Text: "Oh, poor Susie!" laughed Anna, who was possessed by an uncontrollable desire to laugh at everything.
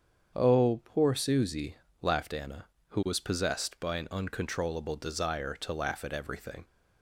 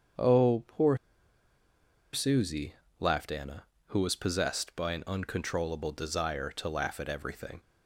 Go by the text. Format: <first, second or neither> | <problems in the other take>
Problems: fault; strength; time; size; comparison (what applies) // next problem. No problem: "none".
first | starts louder than the rest; strong; until 2.3 s; 7.5 dB; strong in the first // pauses between "poor" and "Susie"; at 0.9 s; 1.1 s long